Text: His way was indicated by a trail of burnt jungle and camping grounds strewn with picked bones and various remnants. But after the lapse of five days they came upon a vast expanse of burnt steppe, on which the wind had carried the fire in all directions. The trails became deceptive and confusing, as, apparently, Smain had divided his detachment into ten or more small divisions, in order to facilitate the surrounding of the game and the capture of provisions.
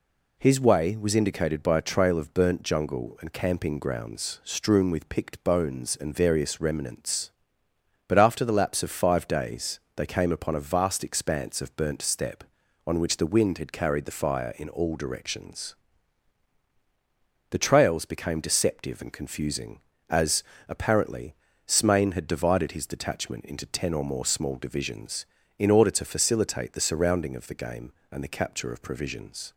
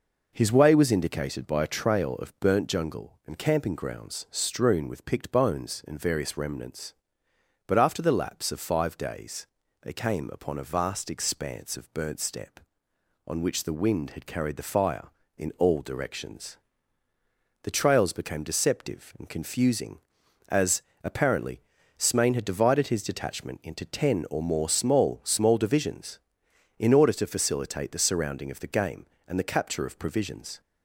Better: first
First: pauses between "days" and "they"; slight; at 9.7 s; 0.16 s long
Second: pauses between "days" and "they"; slight; at 9.4 s; 0.36 s long // says "small" twice; at 25.2 s

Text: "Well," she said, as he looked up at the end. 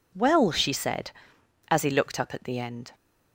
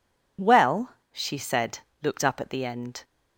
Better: first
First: none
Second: skips "as he"; at 1.9 s

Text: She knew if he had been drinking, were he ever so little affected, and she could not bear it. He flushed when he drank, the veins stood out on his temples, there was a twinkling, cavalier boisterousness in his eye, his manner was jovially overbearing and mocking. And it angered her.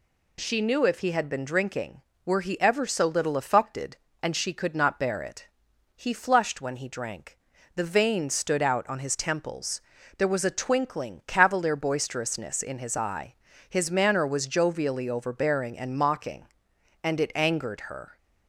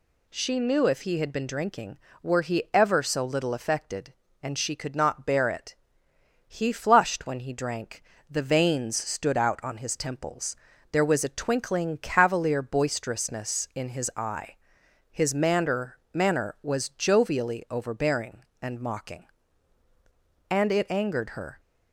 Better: first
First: none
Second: says "manner" twice; at 16.1 s

